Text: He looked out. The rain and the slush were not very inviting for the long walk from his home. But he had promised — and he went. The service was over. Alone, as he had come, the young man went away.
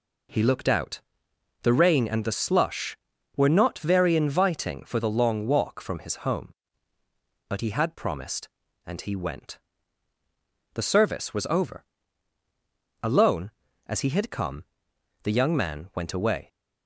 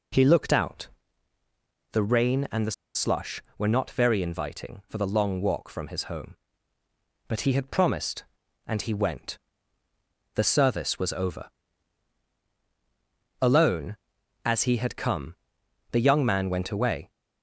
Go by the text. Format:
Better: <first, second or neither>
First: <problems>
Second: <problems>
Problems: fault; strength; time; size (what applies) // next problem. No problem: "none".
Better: first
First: none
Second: pauses between "the" and "slush"; slight; at 2.7 s; 0.23 s long